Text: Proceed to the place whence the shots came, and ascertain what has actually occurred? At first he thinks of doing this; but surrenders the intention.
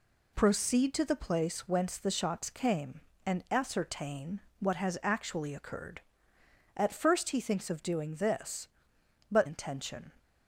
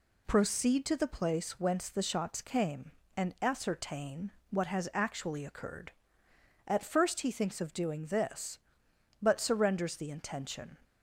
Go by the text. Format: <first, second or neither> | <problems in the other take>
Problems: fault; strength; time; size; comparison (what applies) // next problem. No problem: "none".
second | pauses between "ascertain" and "what"; slight; at 4.4 s; 0.18 s long; slight in the second // skips "surrenders the"; at 9.4 s